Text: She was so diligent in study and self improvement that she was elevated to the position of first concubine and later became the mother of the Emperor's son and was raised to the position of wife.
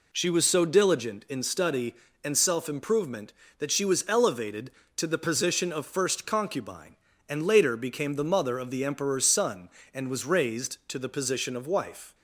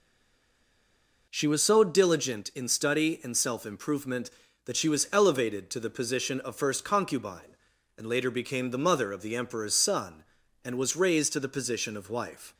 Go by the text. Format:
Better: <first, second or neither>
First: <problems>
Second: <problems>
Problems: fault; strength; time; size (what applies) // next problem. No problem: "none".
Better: first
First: none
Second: stays silent before the first word; noticeable; until 1.2 s; 1.2 s long